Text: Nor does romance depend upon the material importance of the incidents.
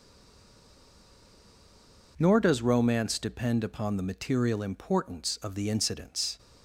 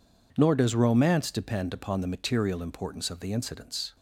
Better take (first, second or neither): second